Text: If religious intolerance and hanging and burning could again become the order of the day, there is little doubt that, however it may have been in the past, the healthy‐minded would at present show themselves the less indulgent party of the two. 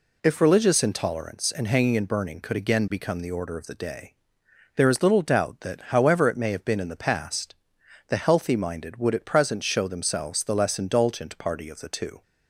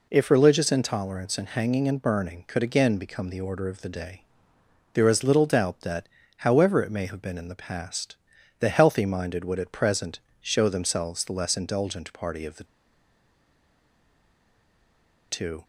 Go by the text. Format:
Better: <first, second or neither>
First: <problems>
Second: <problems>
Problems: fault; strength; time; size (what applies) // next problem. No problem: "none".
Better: first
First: none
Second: pauses between "present" and "show"; slight; at 10.2 s; 0.20 s long // pauses between "the" and "two"; strong; at 12.6 s; 2.6 s long